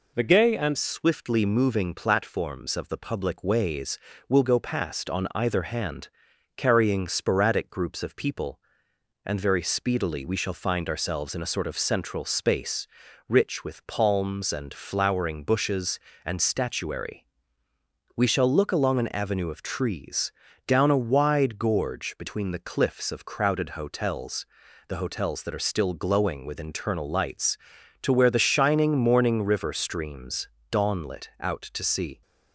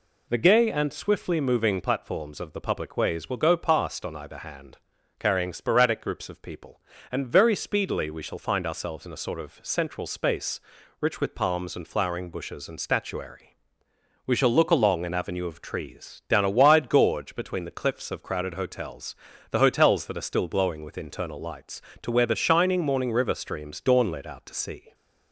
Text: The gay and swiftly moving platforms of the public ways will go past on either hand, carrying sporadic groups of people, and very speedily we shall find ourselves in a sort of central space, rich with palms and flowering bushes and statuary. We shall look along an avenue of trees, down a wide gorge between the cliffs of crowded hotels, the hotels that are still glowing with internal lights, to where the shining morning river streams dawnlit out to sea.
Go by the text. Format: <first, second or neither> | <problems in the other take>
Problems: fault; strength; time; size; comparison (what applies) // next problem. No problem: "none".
second | changes voice at "swiftly"; from 0.7 s on; 31.5 s long // pauses between "streams" and "dawnlit"; slight; at 30.4 s; 0.24 s long